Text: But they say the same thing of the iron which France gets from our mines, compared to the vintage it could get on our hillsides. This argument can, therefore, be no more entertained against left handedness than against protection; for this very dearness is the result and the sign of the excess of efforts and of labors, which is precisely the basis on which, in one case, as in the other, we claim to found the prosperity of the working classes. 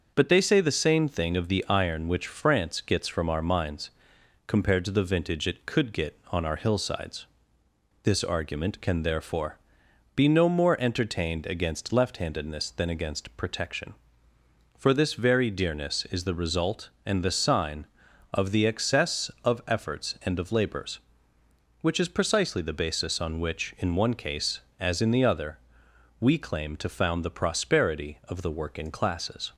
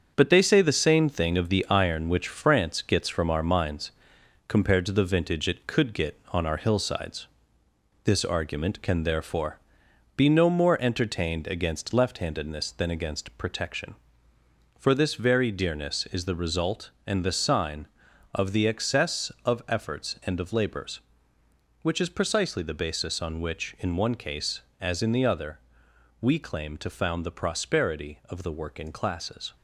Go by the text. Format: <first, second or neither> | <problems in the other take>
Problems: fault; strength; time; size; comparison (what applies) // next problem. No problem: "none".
first | gets quieter; throughout; 6.5 dB // starts louder than the rest; until 1.1 s; 7 dB; noticeable in the first